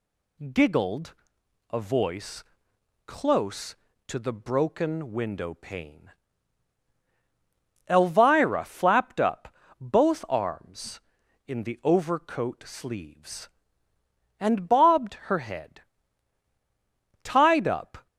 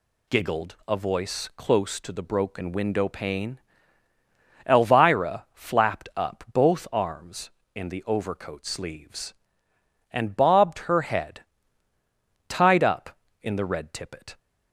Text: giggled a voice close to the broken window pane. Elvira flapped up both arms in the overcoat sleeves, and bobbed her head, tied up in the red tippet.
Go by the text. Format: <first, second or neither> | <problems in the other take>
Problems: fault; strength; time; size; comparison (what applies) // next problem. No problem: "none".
second | pauses between "giggled" and "a"; noticeable; at 1.1 s; 0.58 s long // pauses between "voice" and "close"; noticeable; at 2.4 s; 0.62 s long // pauses between "up" and "both"; slight; at 9.5 s; 0.26 s long // stops before "in the red tippet"; at 18.0 s